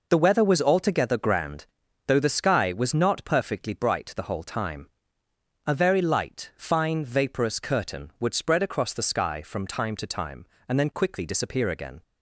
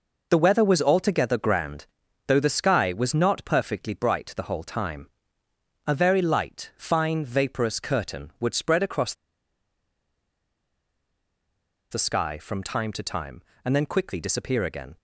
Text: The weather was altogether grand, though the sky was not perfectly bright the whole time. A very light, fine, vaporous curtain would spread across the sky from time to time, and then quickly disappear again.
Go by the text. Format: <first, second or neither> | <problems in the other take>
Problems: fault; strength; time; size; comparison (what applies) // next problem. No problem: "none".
first | pauses between "across" and "the"; strong; at 9.1 s; 2.7 s long